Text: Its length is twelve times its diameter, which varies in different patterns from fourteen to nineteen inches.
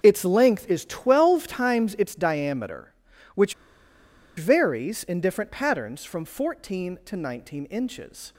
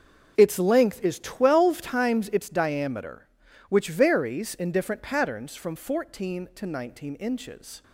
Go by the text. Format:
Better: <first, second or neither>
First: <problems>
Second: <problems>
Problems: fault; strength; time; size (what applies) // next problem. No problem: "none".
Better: second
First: starts louder than the rest; until 1.0 s; 6.5 dB // pauses between "which" and "varies"; noticeable; at 3.5 s; 0.83 s long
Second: starts louder than the rest; until 1.3 s; 6.5 dB